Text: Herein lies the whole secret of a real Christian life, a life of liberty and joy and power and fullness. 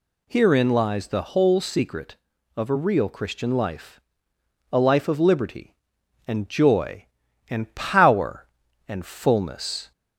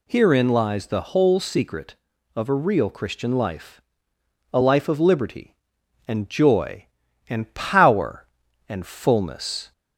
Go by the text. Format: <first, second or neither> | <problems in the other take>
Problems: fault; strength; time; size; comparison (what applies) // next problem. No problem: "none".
neither | none